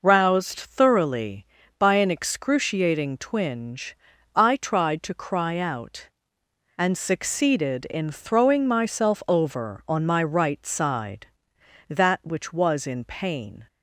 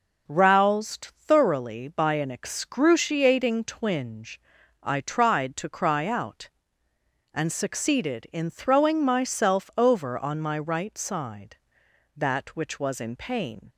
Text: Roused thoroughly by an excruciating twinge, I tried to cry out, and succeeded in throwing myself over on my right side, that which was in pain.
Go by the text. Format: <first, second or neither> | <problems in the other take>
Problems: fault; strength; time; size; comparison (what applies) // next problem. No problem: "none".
neither | none